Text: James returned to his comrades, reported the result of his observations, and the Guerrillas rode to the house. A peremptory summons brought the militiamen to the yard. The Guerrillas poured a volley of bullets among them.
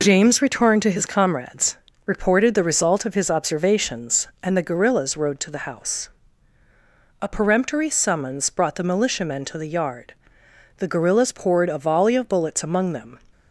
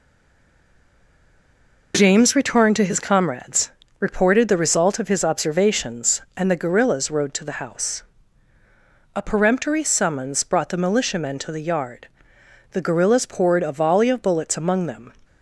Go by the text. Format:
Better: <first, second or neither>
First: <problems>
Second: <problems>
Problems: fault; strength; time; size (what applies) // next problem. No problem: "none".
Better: first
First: none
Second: stays silent before the first word; noticeable; until 1.9 s; 1.9 s long